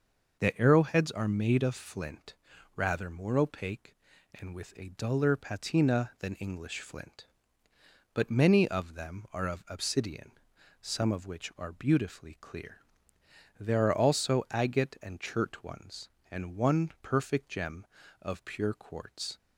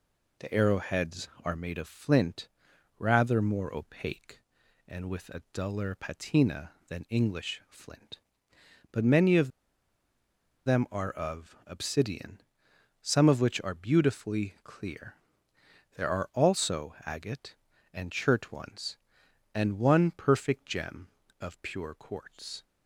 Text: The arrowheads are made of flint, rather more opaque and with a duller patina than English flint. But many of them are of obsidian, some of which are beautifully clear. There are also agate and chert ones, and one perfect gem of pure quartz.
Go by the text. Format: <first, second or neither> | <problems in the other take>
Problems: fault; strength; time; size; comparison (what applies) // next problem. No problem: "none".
first | pauses between "of" and "them"; at 9.4 s; 1.1 s long